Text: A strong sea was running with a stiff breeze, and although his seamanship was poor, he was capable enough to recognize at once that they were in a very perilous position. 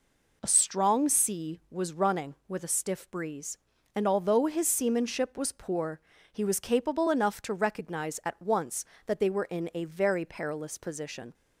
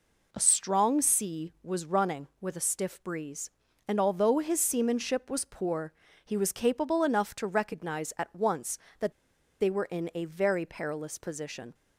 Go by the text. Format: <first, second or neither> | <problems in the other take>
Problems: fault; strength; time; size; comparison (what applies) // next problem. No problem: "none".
first | pauses between "that" and "they"; noticeable; at 9.1 s; 0.47 s long